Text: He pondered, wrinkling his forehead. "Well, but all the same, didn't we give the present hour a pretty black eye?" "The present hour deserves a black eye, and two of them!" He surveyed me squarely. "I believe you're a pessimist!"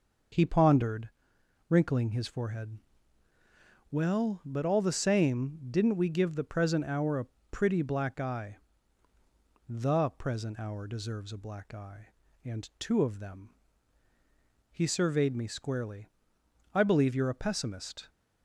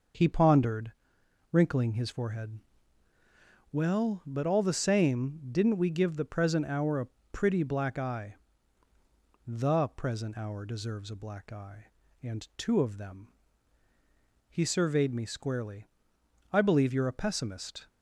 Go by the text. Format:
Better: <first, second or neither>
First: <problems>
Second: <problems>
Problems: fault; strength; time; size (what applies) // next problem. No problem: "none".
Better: neither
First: pauses between "a" and "pretty"; slight; at 7.2 s; 0.24 s long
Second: pauses between "a" and "pretty"; slight; at 7.0 s; 0.24 s long